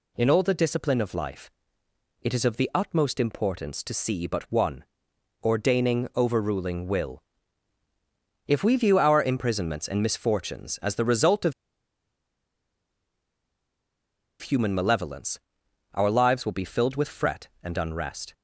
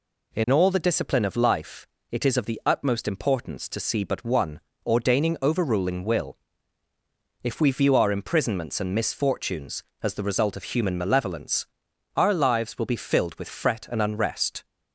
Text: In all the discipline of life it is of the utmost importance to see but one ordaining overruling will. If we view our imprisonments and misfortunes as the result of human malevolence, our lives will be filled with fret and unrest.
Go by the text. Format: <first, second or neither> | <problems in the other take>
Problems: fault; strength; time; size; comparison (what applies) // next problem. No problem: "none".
second | pauses between "life" and "it"; noticeable; at 1.5 s; 0.72 s long; slight in the second // pauses between "one" and "ordaining"; noticeable; at 4.8 s; 0.58 s long; slight in the second // pauses between "of" and "human"; strong; at 11.5 s; 2.8 s long